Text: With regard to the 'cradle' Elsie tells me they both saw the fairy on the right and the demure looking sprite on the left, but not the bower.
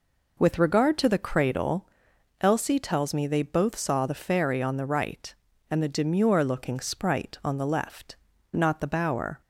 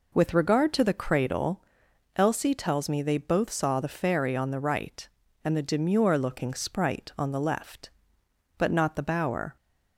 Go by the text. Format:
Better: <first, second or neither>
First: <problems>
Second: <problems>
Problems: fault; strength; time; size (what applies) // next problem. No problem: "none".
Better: second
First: pauses between "cradle" and "Elsie"; noticeable; at 1.8 s; 0.52 s long // skips "but"; at 8.3 s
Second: pauses between "cradle" and "Elsie"; noticeable; at 1.6 s; 0.52 s long